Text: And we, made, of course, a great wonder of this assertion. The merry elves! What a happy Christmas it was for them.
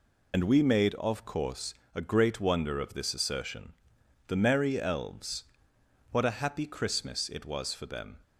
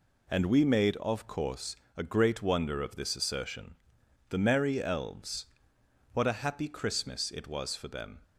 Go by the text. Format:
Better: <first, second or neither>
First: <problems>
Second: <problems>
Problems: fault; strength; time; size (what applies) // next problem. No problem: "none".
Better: second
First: loses the start of "And"; at 0.3 s; 80 ms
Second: none